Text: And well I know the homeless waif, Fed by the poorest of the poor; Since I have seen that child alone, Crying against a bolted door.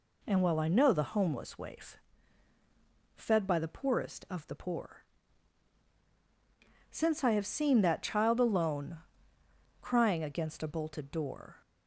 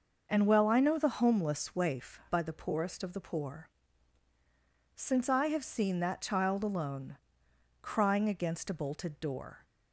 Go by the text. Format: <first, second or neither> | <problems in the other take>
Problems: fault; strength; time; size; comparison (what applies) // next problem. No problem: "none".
first | skips "Fed"; at 2.2 s